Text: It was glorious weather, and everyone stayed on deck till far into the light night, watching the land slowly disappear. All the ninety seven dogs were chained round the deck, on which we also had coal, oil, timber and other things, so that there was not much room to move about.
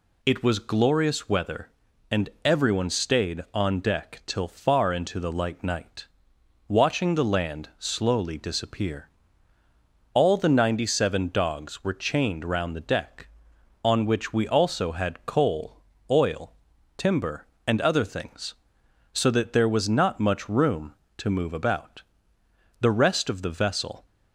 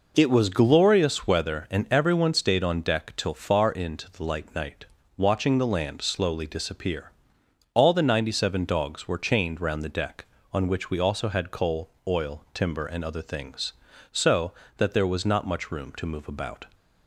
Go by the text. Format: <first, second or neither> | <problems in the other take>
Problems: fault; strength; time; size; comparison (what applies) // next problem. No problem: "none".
second | pauses between "and" and "everyone"; slight; at 2.2 s; 0.16 s long // goes on to say "The rest of the vessel"; noticeable; from 22.8 s on; 1.2 s long